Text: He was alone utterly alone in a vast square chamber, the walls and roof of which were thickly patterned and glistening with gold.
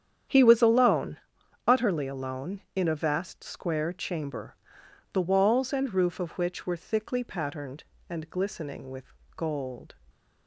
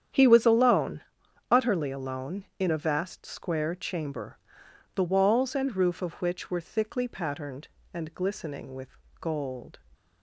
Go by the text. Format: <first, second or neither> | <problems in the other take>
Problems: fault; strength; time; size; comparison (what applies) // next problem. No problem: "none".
neither | starts louder than the rest; strong; the same in both // pauses between "alone" and "utterly"; noticeable; the same in both // pauses between "with" and "gold"; slight; the same in both